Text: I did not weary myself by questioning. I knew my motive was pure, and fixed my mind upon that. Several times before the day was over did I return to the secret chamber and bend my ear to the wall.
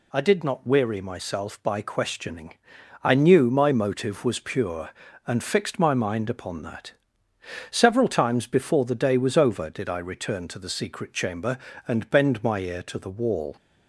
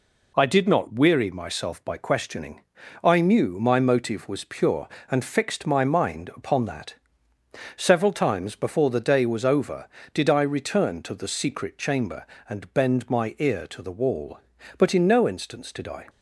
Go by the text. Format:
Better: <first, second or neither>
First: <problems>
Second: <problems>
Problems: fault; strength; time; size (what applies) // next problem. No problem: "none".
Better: first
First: none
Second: goes on to say "But in no instance did I"; noticeable; from 14.7 s on; 1.2 s long